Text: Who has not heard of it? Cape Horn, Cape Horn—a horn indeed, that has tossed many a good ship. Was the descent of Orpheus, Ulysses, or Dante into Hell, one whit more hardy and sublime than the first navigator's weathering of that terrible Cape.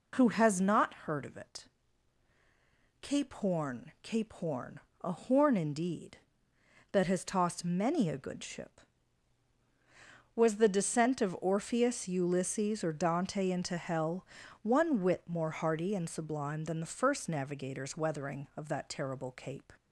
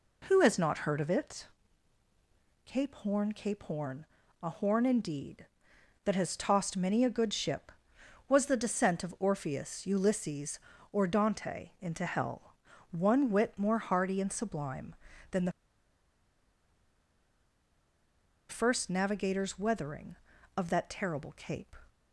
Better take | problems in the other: first | pauses between "the" and "first"; strong; at 15.5 s; 2.9 s long

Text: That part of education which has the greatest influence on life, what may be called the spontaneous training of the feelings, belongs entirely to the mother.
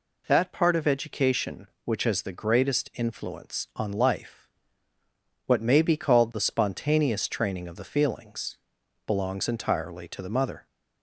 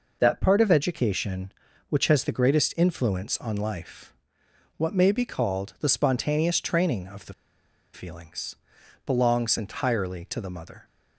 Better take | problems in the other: first | pauses between "the" and "feelings"; noticeable; at 7.3 s; 0.60 s long

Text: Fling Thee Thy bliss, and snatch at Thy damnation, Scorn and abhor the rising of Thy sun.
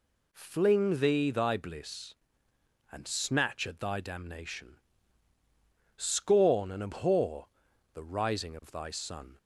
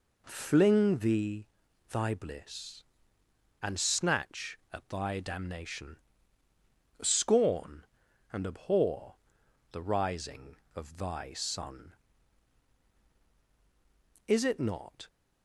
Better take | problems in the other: first | pauses between "Thee" and "Thy"; at 1.4 s; 0.44 s long // pauses between "abhor" and "the"; noticeable; at 9.1 s; 0.56 s long; noticeable in the first // goes on to say "Is it not"; noticeable; from 14.2 s on; 0.80 s long

